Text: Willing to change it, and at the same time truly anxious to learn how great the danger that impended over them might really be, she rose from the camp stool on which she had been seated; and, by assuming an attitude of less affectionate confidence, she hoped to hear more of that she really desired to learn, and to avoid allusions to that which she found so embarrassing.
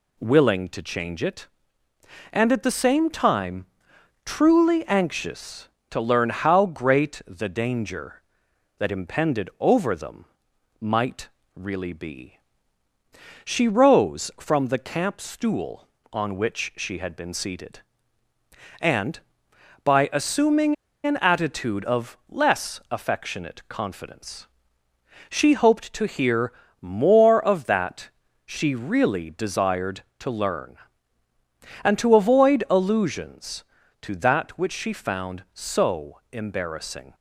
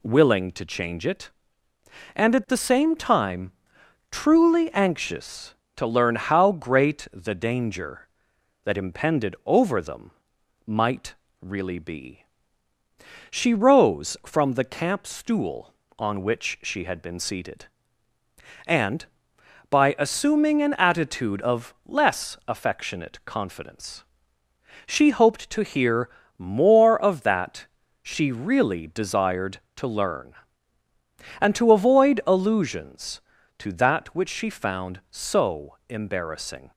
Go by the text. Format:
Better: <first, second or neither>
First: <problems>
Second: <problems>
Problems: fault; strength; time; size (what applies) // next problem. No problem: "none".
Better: second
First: pauses between "time" and "truly"; noticeable; at 3.6 s; 0.58 s long // pauses between "them" and "might"; noticeable; at 10.2 s; 0.56 s long // pauses between "might" and "really"; slight; at 11.2 s; 0.26 s long // pauses between "assuming" and "an"; slight; at 20.7 s; 0.31 s long // pauses between "hear" and "more"; slight; at 26.5 s; 0.30 s long // pauses between "that" and "she"; slight; at 28.1 s; 0.36 s long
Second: pauses between "time" and "truly"; noticeable; at 3.5 s; 0.58 s long // pauses between "them" and "might"; noticeable; at 10.0 s; 0.56 s long // pauses between "might" and "really"; slight; at 11.1 s; 0.26 s long // pauses between "hear" and "more"; slight; at 26.0 s; 0.30 s long // pauses between "that" and "she"; slight; at 27.6 s; 0.36 s long